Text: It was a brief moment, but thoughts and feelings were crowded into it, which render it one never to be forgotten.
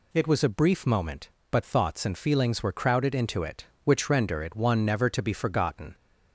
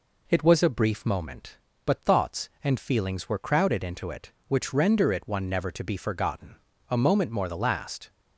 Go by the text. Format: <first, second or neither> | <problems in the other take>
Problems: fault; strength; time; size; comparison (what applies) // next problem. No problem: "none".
first | goes on to say "A moment more the last"; noticeable; from 6.8 s on; 1.2 s long